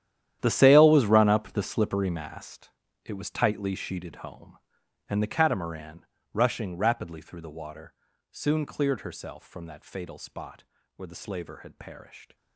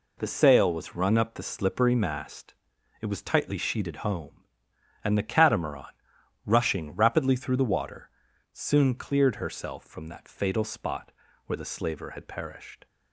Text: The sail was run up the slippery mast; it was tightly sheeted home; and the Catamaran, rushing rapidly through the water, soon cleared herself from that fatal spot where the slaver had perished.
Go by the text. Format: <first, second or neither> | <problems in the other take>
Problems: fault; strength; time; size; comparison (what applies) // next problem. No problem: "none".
second | gets quieter; strong; throughout; 15.5 dB // pauses between "spot" and "where"; slight; at 10.6 s; 0.32 s long; slight in the second